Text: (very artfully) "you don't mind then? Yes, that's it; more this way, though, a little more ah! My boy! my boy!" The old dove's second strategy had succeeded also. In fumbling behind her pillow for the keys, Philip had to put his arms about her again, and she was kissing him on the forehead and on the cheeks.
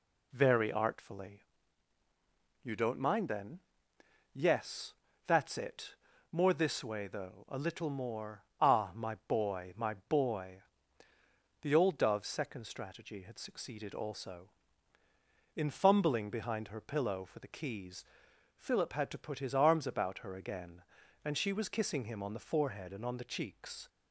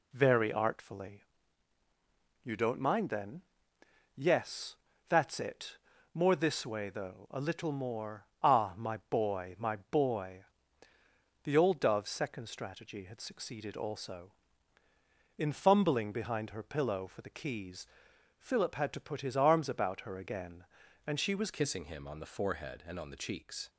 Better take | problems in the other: first | pauses between "more" and "ah"; slight; at 8.2 s; 0.18 s long; slight in the first // changes voice at "kissing"; from 21.5 s on; 2.1 s long

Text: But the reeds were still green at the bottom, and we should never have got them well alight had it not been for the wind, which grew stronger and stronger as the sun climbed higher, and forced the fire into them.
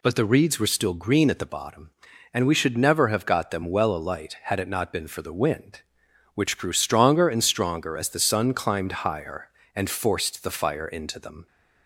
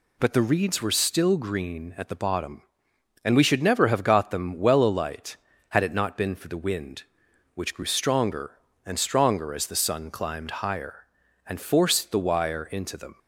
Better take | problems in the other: first | says "wire" for "fire"; at 12.1 s

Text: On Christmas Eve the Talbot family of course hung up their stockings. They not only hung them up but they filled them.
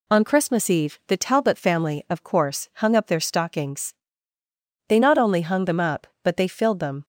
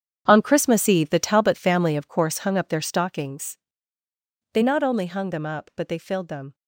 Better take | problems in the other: first | gets quieter; strong; throughout; 12.5 dB

